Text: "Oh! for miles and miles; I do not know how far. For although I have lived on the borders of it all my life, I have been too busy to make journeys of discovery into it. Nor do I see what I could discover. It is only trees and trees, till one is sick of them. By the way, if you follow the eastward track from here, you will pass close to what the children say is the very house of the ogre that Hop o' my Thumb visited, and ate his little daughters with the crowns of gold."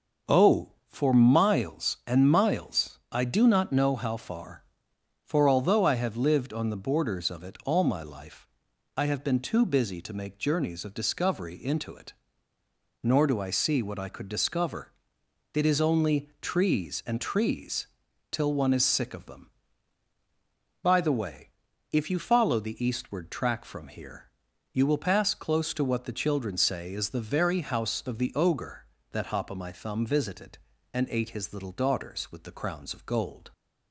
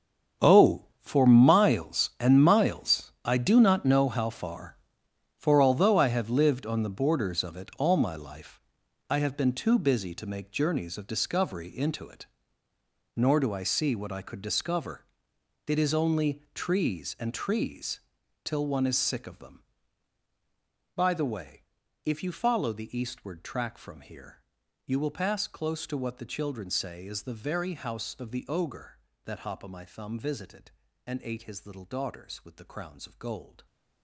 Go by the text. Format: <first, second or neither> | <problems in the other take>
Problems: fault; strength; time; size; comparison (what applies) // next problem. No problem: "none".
first | gets quieter; strong; throughout; 14.5 dB